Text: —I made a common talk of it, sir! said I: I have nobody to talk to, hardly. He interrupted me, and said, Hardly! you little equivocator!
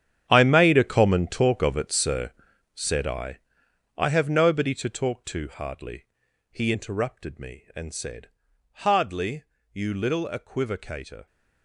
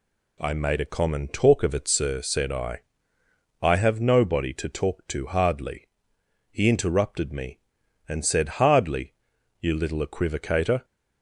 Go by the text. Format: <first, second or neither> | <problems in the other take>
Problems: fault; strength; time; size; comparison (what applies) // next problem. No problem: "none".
second | gets quieter; strong; throughout; 14 dB